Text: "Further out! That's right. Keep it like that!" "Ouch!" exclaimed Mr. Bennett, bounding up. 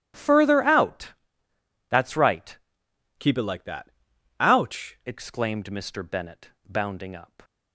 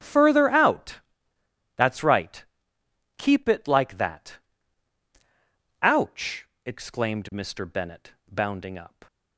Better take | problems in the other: second | starts louder than the rest; strong; until 1.9 s; 12.5 dB; strong in the second // changes voice from "Keep" to "Ouch"; from 3.1 to 4.9 s; 1.8 s long

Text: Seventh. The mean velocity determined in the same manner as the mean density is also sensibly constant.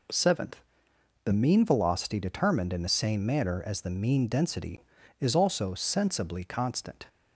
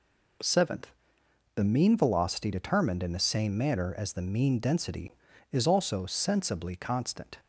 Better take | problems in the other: neither | none

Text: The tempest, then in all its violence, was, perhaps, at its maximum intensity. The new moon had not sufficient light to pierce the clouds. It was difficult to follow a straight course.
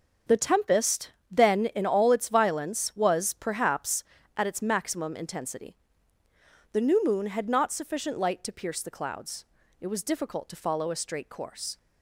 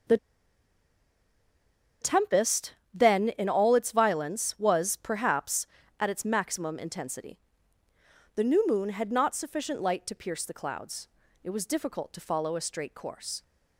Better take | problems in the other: first | starts louder than the rest; until 3.1 s; 6.5 dB; also in the first // pauses between "The" and "tempest"; strong; at 0.1 s; 1.8 s long

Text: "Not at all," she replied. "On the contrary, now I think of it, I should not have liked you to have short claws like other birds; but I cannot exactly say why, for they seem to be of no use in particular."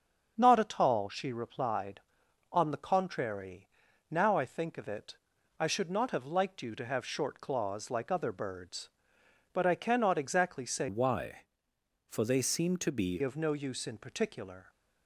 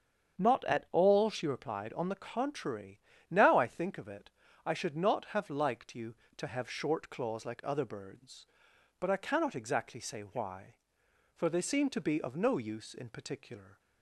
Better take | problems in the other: second | starts louder than the rest; until 1.4 s; 6.5 dB; strong in the second // changes voice from "why" to "be"; from 10.8 to 13.1 s; 2.3 s long

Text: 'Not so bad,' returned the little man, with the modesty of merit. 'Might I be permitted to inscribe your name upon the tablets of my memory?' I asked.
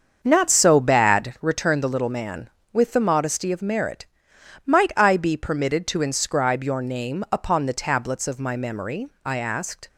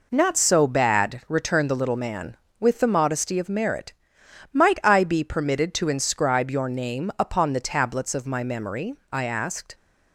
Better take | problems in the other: second | starts louder than the rest; until 1.6 s; 6.5 dB

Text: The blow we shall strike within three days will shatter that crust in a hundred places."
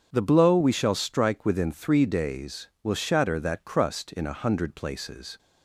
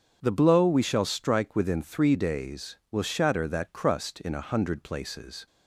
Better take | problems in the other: neither | starts louder than the rest; strong; the same in both

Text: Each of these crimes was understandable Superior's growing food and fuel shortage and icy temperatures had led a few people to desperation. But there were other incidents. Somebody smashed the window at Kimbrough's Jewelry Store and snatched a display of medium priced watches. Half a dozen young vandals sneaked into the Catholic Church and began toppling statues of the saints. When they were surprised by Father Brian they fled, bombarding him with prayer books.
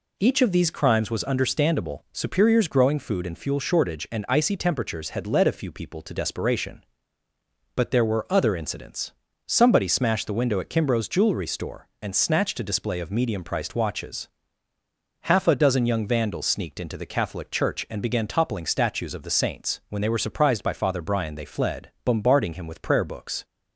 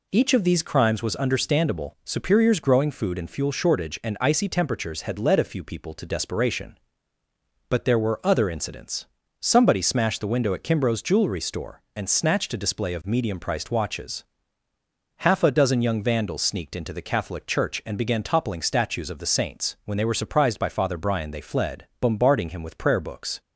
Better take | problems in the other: neither | none

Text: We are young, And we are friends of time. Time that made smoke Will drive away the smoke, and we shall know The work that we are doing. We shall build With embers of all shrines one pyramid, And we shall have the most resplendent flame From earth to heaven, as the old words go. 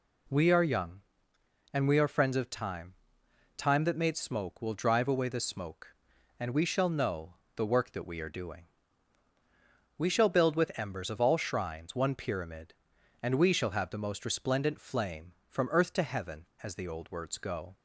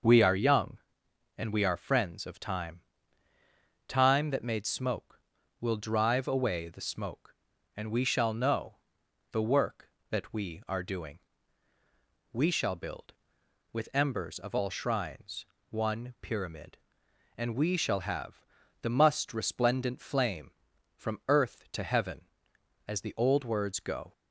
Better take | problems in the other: first | starts louder than the rest; noticeable; until 1.6 s; 6 dB // pauses between "know" and "The"; noticeable; at 8.7 s; 0.56 s long; slight in the first // pauses between "shrines" and "one"; slight; at 15.4 s; 0.24 s long // pauses between "have" and "the"; at 18.4 s; 0.40 s long // says "must" for "most"; at 18.9 s

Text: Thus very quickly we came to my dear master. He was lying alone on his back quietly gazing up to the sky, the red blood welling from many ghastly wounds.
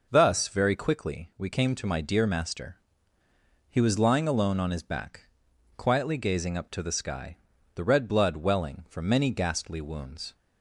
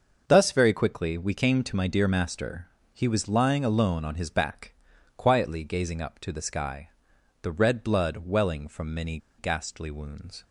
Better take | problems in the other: first | starts louder than the rest; noticeable; until 1.2 s; 6 dB // pauses between "back" and "quietly"; noticeable; at 4.7 s; 0.46 s long; noticeable in the first // pauses between "many" and "ghastly"; slight; at 9.1 s; 0.20 s long

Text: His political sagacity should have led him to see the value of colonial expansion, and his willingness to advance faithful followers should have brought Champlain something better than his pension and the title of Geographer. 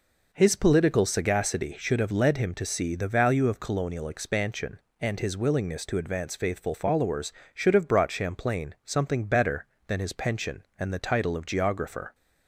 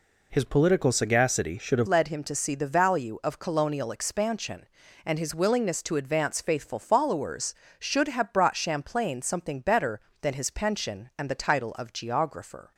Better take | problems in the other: first | changes voice at "led"; from 1.8 s on; 10.9 s long

